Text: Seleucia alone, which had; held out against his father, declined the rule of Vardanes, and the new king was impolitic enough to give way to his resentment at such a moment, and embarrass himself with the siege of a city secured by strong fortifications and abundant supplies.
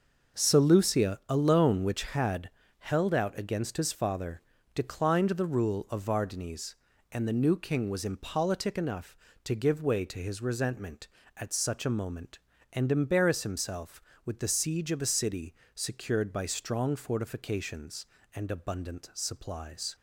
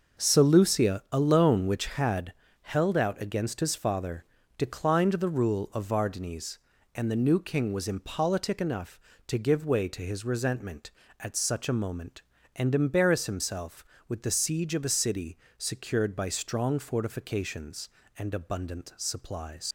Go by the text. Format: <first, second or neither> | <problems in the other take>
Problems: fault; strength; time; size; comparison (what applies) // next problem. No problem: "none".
first | starts louder than the rest; noticeable; until 1.3 s; 6 dB; noticeable in the first // pauses between "city" and "secured"; slight; at 15.3 s; 0.18 s long; slight in the first // leaves "supplies" unfinished; at 19.6 s; 70 ms